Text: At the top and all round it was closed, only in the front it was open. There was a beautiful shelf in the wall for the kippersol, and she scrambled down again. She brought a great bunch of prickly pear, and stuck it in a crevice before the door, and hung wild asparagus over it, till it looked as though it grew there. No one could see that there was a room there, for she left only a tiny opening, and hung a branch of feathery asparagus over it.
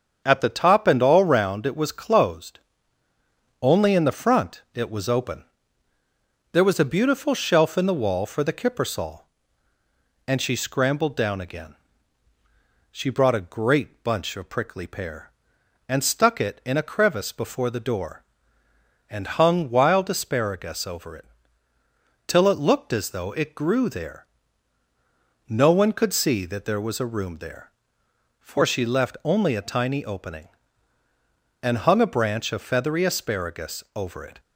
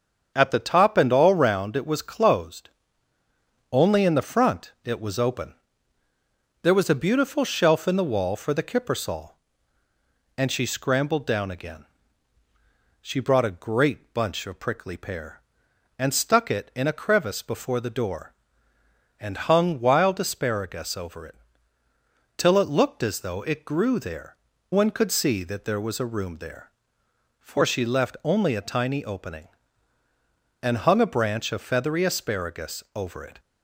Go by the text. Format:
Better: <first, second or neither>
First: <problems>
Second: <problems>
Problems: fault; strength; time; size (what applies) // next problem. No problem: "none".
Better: first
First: starts louder than the rest; until 1.2 s; 6.5 dB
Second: starts louder than the rest; until 1.3 s; 7 dB // skips "No"; at 24.5 s